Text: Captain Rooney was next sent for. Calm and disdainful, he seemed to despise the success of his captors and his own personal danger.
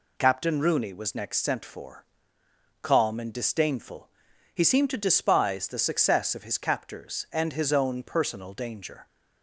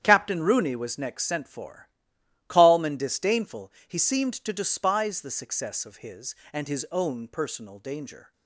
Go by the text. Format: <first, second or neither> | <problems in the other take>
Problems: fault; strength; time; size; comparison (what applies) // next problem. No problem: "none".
first | starts louder than the rest; strong; until 1.0 s; 9.5 dB // skips "captors"; at 6.4 s